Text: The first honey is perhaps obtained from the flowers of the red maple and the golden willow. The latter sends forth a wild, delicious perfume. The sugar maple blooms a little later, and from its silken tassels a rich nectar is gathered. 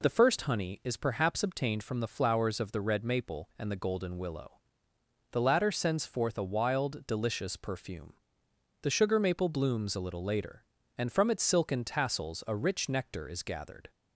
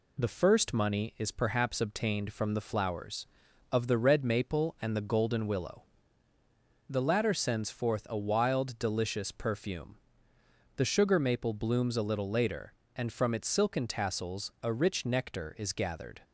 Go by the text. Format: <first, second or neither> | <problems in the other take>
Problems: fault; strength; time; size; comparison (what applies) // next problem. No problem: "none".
first | says "money" for "honey"; at 0.7 s